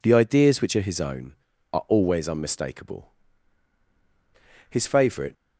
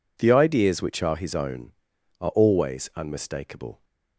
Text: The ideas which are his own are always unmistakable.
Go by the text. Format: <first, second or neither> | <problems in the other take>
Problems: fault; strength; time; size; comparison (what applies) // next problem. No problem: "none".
second | goes on to say "His favourite"; noticeable; from 4.6 s on; 0.64 s long